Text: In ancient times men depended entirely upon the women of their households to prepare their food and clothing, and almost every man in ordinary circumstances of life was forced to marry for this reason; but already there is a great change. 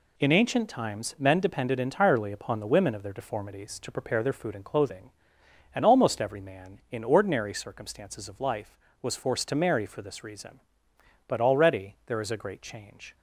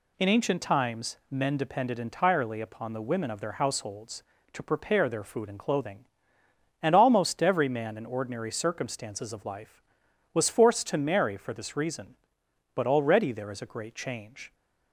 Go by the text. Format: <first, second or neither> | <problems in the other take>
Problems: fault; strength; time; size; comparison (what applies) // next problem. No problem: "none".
second | says "deformities" for "households"; at 3.1 s